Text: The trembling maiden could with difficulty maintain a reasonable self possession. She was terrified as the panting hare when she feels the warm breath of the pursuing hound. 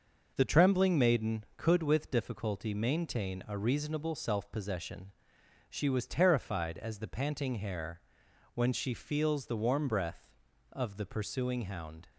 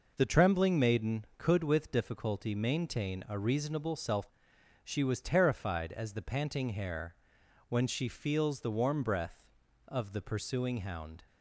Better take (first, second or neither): first